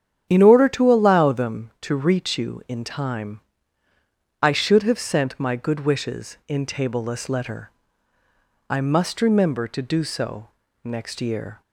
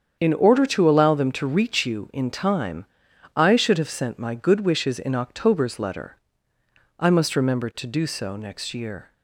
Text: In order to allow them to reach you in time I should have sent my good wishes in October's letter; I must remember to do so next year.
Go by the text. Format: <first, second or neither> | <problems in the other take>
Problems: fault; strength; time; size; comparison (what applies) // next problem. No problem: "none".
second | starts louder than the rest; strong; until 1.3 s; 9.5 dB; strong in the second // pauses between "time" and "I"; at 3.3 s; 1.0 s long; noticeable in the second // says "Tableless" for "October's"; at 6.6 s // pauses between "so" and "next"; slight; at 10.4 s; 0.34 s long